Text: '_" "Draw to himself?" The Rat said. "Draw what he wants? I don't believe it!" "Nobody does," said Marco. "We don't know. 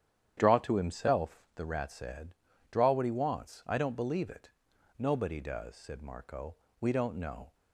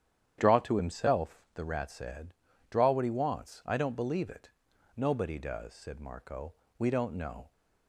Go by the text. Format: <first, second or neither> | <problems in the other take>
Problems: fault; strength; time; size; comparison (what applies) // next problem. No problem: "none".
neither | starts louder than the rest; strong; the same in both